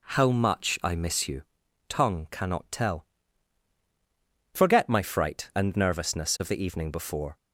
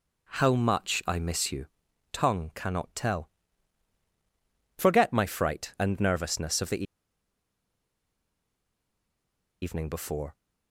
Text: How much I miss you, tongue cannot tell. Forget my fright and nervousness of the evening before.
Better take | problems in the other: first | pauses between "the" and "evening"; strong; at 6.8 s; 2.7 s long

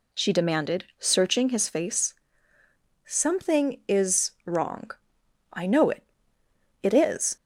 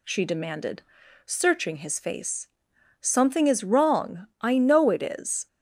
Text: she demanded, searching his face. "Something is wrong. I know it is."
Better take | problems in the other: second | says "it" twice; at 6.8 s

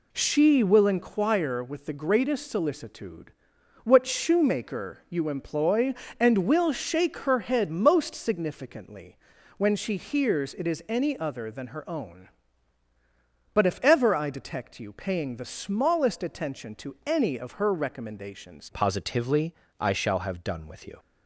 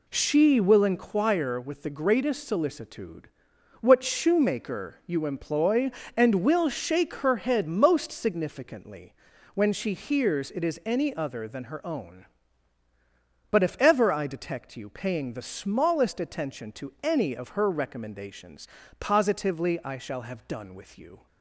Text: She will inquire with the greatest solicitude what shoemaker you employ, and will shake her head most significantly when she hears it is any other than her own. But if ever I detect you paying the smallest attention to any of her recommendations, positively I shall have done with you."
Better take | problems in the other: second | pauses between "solicitude" and "what"; noticeable; at 3.3 s; 0.52 s long; noticeable in the second // pauses between "significantly" and "when"; at 9.1 s; 0.40 s long; also in the second // changes voice at "positively"; from 18.7 s on; 2.2 s long // pauses between "positively" and "I"; slight; at 19.5 s; 0.26 s long

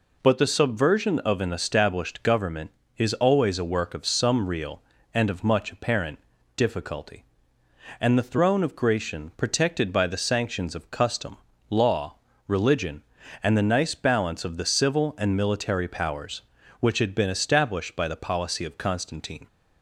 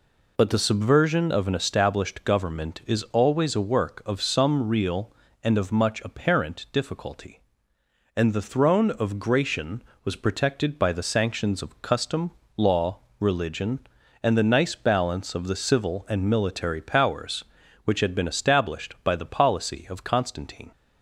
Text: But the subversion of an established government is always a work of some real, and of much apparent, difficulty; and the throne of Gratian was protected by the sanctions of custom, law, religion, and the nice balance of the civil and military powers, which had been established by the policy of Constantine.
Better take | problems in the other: second | skips "was"; at 9.3 s

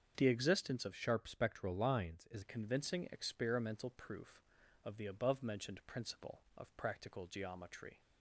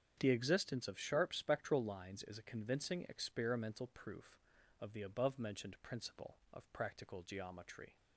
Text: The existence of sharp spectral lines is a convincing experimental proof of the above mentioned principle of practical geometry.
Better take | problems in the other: second | starts louder than the rest; strong; until 1.1 s; 7 dB; strong in the second // changes voice from "sharp" to "is"; from 0.9 to 2.4 s; 1.5 s long

